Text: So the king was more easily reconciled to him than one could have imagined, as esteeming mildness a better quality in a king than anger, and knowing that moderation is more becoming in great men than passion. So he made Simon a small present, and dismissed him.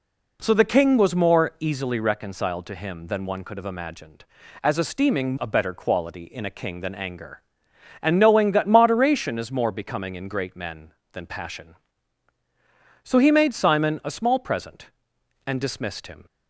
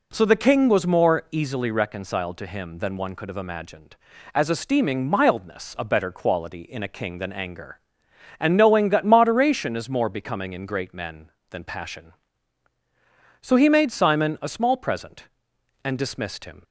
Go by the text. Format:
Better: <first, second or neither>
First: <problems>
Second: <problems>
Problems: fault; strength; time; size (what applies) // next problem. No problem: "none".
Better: second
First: skips "mildness"; at 5.3 s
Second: none